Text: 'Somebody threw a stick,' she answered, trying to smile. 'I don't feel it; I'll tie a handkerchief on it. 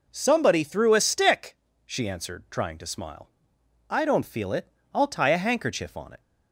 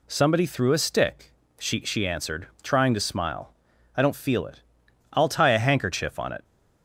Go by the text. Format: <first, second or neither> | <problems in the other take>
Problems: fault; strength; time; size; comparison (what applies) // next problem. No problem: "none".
first | says "she" twice; at 1.8 s